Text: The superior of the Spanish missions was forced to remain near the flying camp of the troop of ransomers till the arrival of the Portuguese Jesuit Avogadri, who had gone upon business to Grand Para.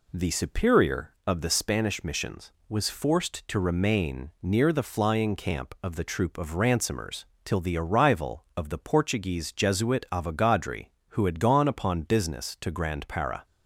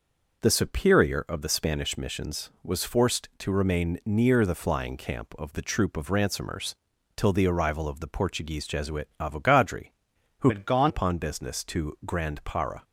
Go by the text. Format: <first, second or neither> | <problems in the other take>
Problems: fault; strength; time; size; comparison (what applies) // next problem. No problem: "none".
first | pauses between "ransomers" and "till"; at 6.7 s; 0.40 s long; slight in the first // changes voice from "had" to "gone"; from 10.4 to 10.9 s; 0.5 s long